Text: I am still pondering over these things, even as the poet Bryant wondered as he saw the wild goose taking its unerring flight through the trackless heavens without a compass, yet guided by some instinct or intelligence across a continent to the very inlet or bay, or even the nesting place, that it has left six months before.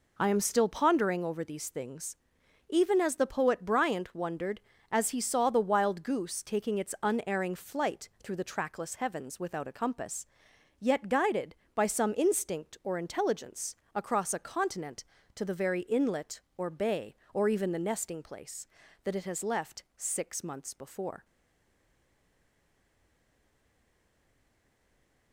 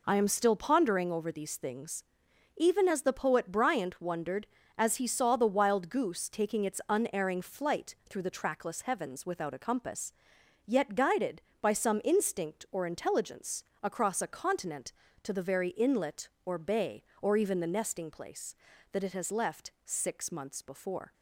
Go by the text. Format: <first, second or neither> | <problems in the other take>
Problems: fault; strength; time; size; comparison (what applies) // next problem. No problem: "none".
second | pauses between "intelligence" and "across"; slight; at 13.7 s; 0.18 s long; slight in the second // stays silent after the last word; strong; from 21.2 s on; 4.1 s long